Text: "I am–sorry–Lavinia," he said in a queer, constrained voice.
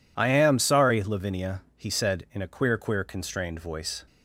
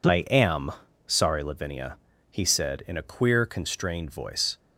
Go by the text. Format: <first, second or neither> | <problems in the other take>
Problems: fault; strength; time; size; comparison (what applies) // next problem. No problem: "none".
second | says "queer" twice; at 2.7 s